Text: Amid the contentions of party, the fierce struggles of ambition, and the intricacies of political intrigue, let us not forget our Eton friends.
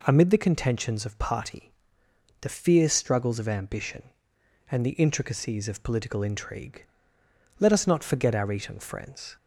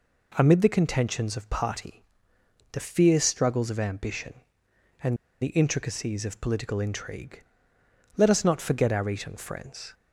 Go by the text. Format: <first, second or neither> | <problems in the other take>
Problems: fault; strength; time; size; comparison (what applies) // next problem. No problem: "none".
first | pauses between "and" and "the"; slight; at 5.1 s; 0.26 s long